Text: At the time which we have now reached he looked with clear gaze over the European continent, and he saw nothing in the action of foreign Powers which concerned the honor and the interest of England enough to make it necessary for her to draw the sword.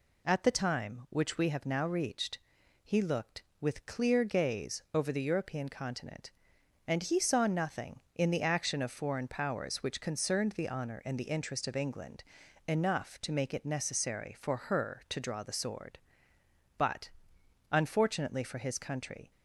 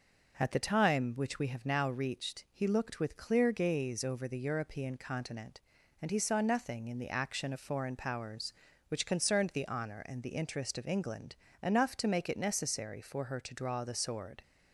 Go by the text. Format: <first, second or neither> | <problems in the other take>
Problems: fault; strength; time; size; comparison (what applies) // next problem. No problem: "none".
second | pauses between "reached" and "he"; noticeable; at 2.3 s; 0.46 s long // pauses between "England" and "enough"; at 12.2 s; 0.44 s long; slight in the second // goes on to say "But unfortunately for his country"; strong; from 16.7 s on; 2.5 s long